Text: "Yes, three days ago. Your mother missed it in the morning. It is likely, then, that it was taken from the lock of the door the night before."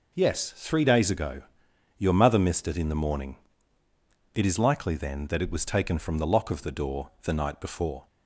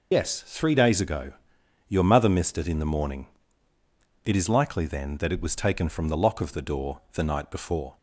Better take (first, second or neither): first